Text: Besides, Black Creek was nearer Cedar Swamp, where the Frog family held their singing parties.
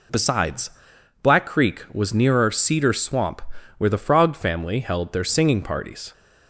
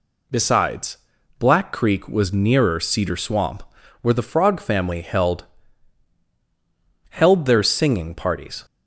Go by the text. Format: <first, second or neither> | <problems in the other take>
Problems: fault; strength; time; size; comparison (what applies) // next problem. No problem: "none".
first | says "held" twice; at 7.1 s